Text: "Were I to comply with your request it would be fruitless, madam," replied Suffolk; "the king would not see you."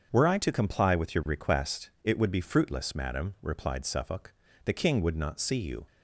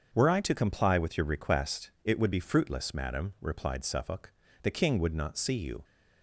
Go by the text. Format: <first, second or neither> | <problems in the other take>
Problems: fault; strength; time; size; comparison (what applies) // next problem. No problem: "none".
neither | starts louder than the rest; the same in both // pauses between "request" and "it"; slight; the same in both